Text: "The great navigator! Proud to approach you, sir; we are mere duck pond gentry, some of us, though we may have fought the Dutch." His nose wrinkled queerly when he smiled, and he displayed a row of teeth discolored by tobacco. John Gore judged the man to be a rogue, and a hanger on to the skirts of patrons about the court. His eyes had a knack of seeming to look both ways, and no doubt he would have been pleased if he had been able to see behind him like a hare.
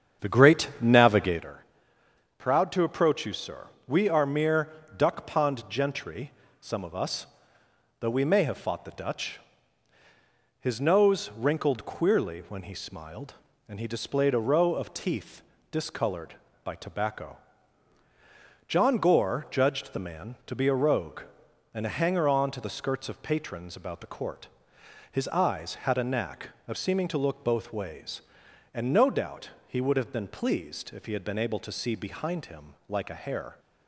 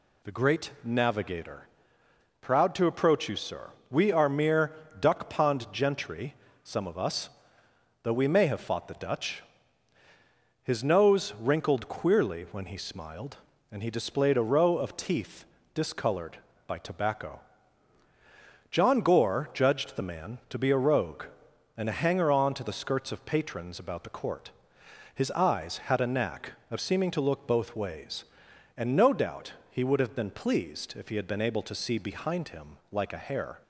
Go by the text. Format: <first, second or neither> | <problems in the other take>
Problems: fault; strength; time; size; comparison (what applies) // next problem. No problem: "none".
second | starts louder than the rest; strong; until 1.5 s; 8 dB // pauses between "mere" and "duck"; slight; at 4.6 s; 0.28 s long; slight in the second // pauses between "teeth" and "discolored"; slight; at 15.4 s; 0.30 s long; slight in the second // pauses between "doubt" and "he"; slight; at 29.5 s; 0.16 s long; slight in the second